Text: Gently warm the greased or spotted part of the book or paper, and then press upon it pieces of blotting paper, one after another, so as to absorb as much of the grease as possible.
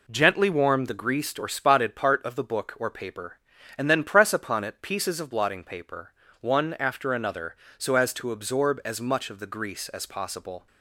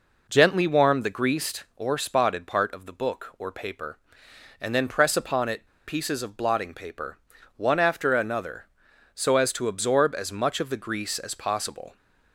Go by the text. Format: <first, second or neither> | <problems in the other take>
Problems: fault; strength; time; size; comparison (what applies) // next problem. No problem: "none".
first | pauses between "it" and "pieces"; slight; at 5.6 s; 0.19 s long